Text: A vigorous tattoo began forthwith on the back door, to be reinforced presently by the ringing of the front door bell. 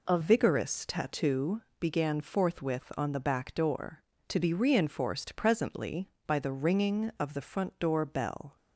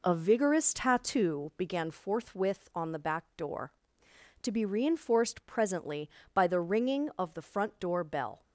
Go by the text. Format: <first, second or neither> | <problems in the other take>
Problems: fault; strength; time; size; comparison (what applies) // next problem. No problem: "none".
second | changes voice at "vigorous"; from 0.2 s on; 8.3 s long // pauses between "tattoo" and "began"; slight; at 1.6 s; 0.18 s long